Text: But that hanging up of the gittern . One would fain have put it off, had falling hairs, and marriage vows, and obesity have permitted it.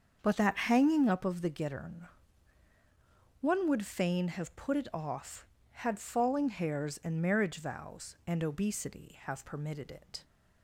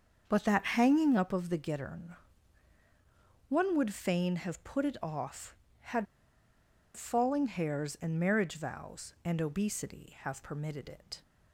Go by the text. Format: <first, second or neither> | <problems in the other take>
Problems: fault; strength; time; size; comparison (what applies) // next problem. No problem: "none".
first | starts louder than the rest; until 1.3 s; 7 dB; also in the first // pauses between "had" and "falling"; noticeable; at 6.0 s; 0.90 s long